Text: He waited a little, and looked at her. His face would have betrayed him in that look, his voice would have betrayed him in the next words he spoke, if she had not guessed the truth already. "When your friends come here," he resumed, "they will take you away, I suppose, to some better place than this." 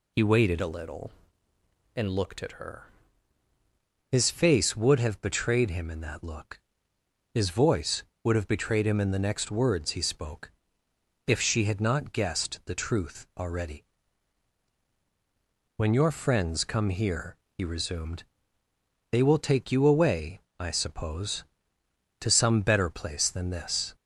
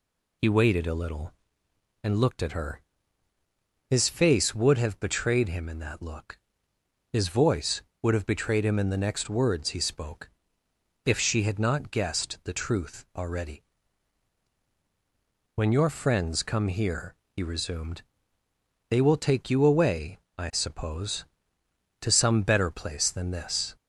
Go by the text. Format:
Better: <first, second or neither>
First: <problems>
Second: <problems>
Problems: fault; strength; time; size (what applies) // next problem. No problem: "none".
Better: second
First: changes voice from "a" to "her"; from 0.5 to 2.8 s; 2.3 s long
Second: none